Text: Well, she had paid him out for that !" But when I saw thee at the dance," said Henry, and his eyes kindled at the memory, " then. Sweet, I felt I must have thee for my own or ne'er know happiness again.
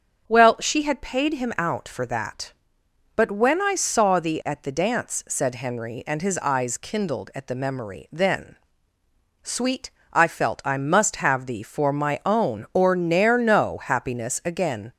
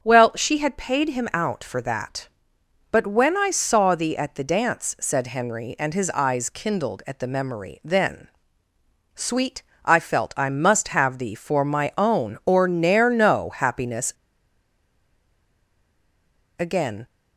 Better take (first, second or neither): first